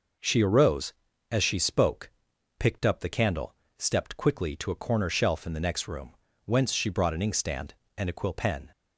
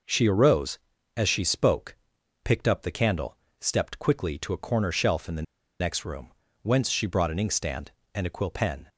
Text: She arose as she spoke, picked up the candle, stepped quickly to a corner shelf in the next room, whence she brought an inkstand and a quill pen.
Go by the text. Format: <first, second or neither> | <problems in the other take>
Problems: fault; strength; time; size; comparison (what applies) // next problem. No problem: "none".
first | pauses between "the" and "next"; at 5.4 s; 0.37 s long